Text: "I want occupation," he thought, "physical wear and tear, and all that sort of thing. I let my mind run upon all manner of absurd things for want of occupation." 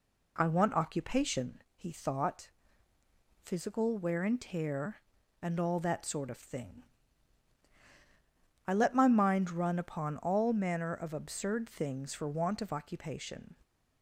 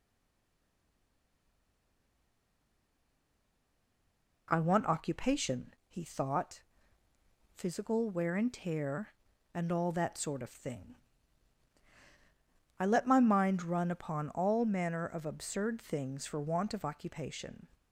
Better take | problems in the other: first | stays silent before the first word; strong; until 4.4 s; 4.4 s long

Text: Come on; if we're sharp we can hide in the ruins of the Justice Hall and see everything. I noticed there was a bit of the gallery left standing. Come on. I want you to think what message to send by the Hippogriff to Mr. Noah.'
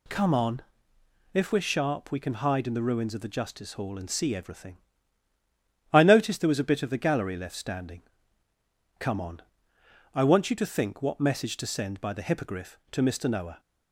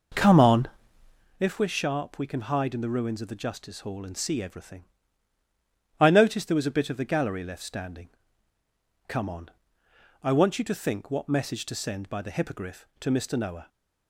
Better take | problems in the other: first | starts louder than the rest; noticeable; until 1.4 s; 5.5 dB

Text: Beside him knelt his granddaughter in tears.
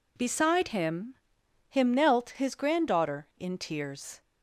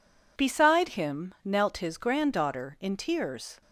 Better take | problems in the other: second | says "him" twice; at 1.6 s

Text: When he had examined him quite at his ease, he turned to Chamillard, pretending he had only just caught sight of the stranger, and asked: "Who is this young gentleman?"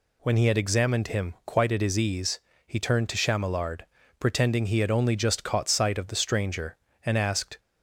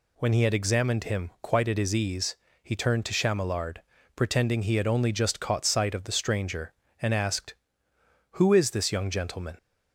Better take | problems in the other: second | stops before "Who is this young gentleman"; at 7.5 s

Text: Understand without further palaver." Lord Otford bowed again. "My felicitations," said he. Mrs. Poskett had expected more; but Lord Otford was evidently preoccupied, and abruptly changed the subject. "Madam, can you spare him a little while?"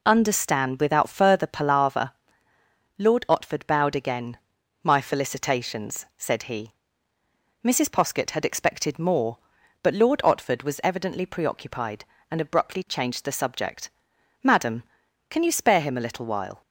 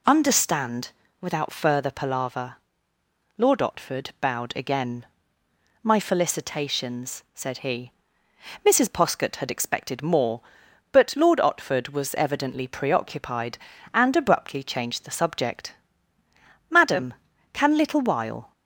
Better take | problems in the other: first | pauses between "Understand" and "without"; slight; at 0.9 s; 0.30 s long // skips "you spare him a"; at 17.7 s

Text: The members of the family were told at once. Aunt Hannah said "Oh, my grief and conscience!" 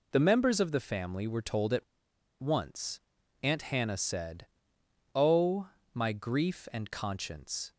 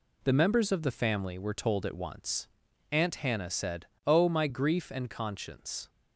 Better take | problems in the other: second | pauses between "at" and "once"; noticeable; at 1.8 s; 0.57 s long // pauses between "said" and "Oh"; noticeable; at 4.4 s; 0.66 s long; slight in the second

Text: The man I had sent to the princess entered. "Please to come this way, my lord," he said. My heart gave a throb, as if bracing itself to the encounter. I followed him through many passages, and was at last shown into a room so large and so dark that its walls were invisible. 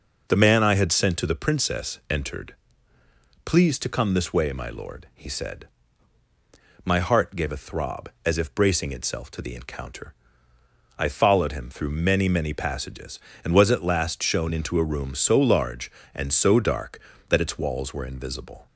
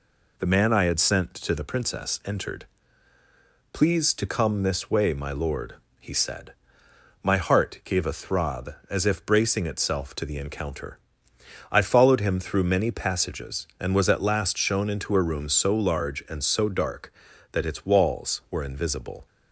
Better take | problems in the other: second | says "many" twice; at 12.2 s

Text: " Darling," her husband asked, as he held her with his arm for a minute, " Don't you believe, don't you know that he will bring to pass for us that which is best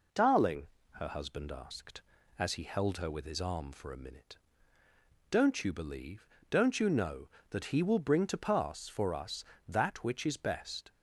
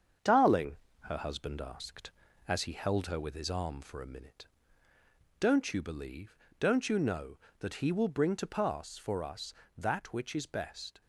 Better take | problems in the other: first | gets quieter; slight; throughout; 2.5 dB

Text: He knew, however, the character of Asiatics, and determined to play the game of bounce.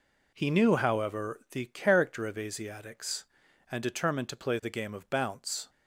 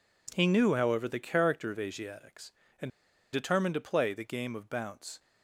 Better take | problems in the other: first | pauses between "and" and "determined"; at 2.9 s; 0.43 s long

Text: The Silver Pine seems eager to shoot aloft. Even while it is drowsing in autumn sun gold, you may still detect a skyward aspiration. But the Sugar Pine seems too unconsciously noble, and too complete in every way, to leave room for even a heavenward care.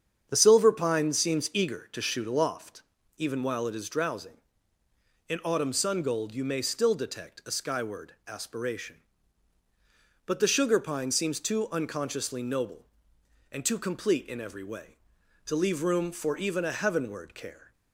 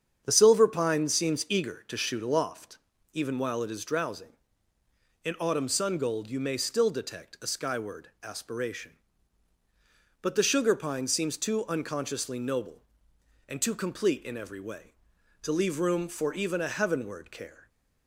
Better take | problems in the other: neither | starts louder than the rest; strong; the same in both // pauses between "skyward" and "aspiration"; slight; the same in both

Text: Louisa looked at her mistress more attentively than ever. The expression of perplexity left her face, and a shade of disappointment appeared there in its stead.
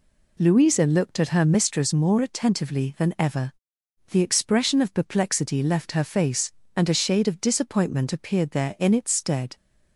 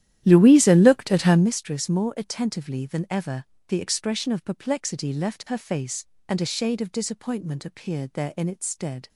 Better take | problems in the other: first | starts louder than the rest; strong; until 1.5 s; 12 dB

